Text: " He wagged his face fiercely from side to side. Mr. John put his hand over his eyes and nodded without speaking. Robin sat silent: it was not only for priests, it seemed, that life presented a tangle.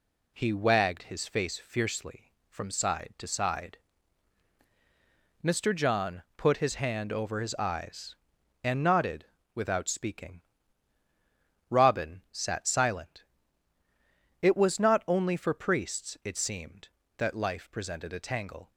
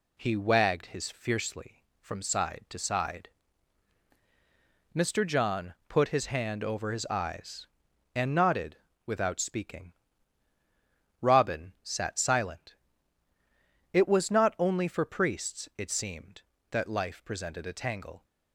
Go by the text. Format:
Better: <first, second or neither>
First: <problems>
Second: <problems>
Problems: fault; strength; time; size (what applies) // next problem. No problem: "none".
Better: first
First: pauses between "nodded" and "without"; slight; at 9.2 s; 0.28 s long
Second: skips "face"; at 1.1 s // pauses between "nodded" and "without"; slight; at 8.7 s; 0.28 s long